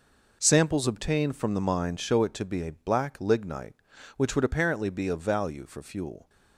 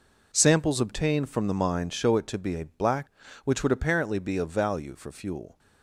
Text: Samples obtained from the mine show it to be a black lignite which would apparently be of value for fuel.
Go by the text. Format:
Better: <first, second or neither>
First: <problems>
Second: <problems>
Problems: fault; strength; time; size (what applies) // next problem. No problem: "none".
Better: first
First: none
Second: skips "lignite"; at 3.2 s